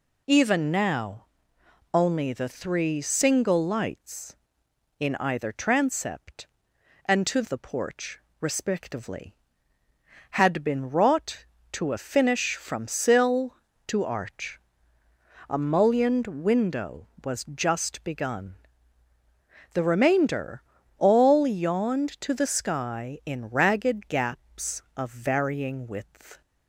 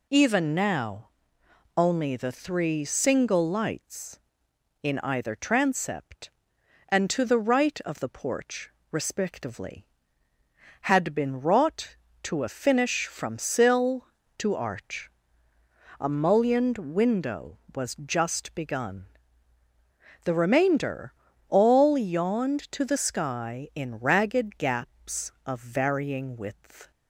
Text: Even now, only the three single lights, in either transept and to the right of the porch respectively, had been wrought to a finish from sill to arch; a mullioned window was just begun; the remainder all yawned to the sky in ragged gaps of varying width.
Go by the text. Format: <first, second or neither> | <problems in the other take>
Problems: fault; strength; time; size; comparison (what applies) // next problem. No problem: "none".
second | skips "the right of"; at 7.4 s // pauses between "porch" and "respectively"; slight; at 8.1 s; 0.22 s long; slight in the second // pauses between "remainder" and "all"; slight; at 20.6 s; 0.34 s long; slight in the second